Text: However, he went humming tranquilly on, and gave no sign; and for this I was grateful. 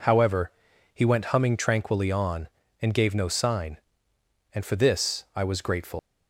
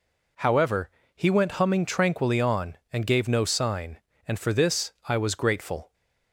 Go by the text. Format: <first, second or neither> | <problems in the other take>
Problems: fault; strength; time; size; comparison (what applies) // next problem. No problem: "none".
second | leaves "grateful" unfinished; at 5.9 s; 120 ms